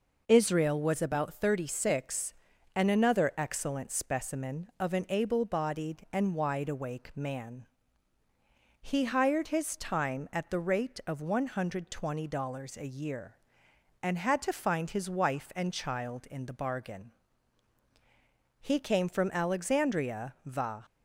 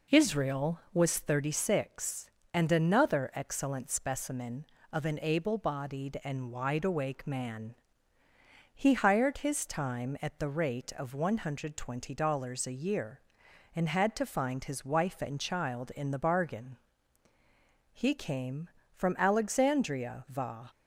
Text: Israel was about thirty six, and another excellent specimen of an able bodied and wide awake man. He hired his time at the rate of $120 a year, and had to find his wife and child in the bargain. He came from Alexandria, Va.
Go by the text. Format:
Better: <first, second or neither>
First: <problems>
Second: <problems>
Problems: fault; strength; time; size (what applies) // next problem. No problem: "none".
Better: first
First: none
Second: skips "about"; at 1.1 s